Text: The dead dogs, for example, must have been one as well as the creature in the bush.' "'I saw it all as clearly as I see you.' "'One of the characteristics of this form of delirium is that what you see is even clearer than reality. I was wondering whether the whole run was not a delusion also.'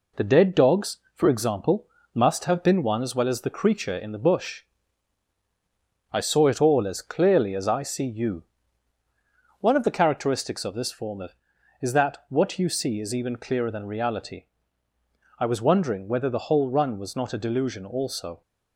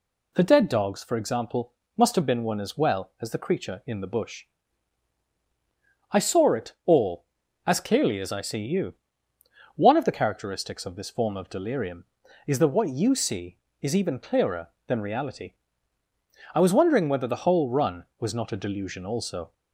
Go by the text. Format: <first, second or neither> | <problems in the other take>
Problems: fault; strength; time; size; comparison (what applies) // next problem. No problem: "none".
second | skips "delirium"; at 11.5 s